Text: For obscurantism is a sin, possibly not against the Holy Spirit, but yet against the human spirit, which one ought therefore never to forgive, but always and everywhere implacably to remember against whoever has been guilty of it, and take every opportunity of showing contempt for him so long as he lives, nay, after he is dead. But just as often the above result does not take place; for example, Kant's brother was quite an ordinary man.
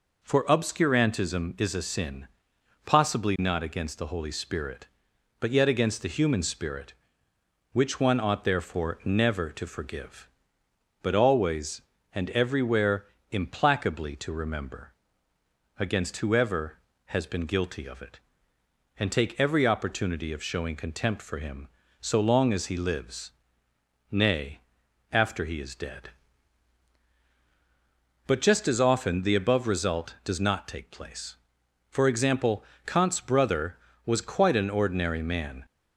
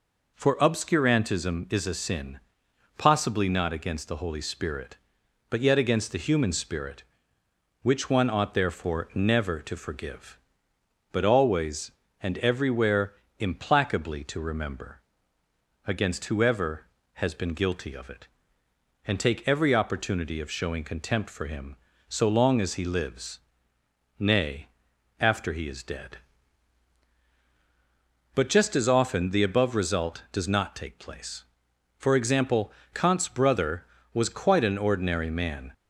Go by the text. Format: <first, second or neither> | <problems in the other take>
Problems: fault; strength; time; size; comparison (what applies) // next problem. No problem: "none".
neither | pauses between "everywhere" and "implacably"; slight; the same in both // pauses between "remember" and "against"; noticeable; the same in both